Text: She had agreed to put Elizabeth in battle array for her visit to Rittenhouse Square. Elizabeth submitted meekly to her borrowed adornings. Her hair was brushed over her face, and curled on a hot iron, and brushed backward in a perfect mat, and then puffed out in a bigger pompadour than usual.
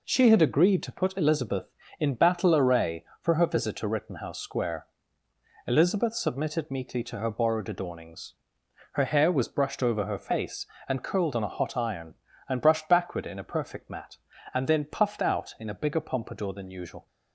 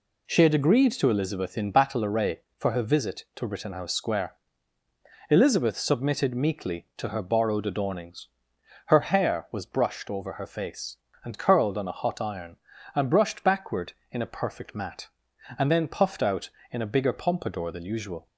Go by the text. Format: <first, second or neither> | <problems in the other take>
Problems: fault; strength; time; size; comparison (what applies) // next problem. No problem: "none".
first | skips "put"; at 1.0 s